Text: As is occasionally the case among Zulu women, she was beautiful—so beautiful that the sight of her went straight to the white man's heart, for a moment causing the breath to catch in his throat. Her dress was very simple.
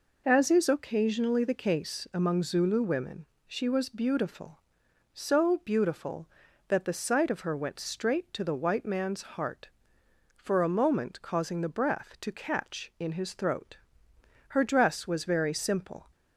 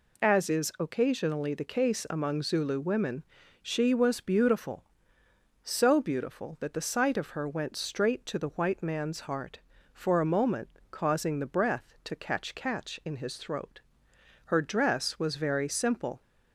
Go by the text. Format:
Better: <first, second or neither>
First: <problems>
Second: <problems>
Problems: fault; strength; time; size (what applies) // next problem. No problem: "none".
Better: first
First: none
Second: pauses between "moment" and "causing"; slight; at 10.6 s; 0.22 s long // says "catch" twice; at 12.5 s